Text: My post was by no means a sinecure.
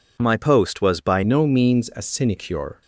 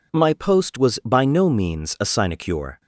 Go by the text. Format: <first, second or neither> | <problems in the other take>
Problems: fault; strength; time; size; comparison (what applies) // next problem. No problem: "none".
second | changes voice at "no"; from 1.2 s on; 1.6 s long